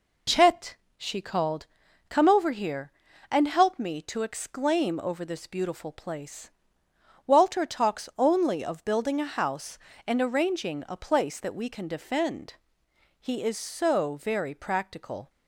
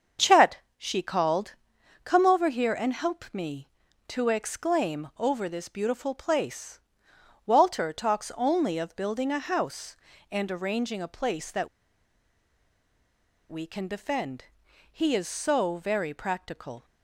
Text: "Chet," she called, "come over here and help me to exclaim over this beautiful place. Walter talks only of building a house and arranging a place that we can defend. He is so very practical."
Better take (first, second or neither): first